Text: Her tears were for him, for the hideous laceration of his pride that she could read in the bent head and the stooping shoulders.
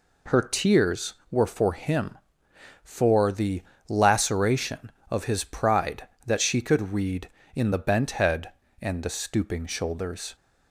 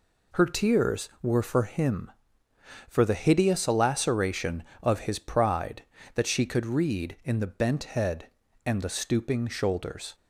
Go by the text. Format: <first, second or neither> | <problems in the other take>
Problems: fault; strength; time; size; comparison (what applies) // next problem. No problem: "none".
second | skips "hideous"; at 3.7 s